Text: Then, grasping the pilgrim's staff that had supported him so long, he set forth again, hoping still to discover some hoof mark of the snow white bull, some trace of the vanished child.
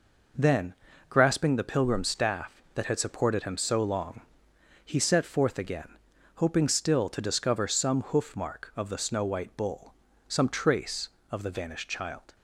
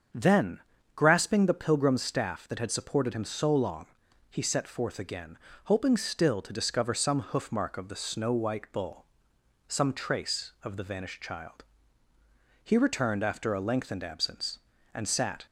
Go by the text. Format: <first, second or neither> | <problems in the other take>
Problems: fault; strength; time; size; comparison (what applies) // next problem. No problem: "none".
first | starts louder than the rest; until 1.5 s; 7 dB // goes on to say "He returned after a lengthened absence and sat"; strong; from 12.6 s on; 2.8 s long